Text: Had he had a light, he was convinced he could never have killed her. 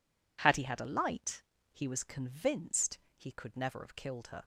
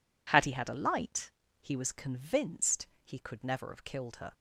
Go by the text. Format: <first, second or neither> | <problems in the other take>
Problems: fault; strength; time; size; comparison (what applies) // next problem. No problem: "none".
neither | pauses between "convinced" and "he"; slight; the same in both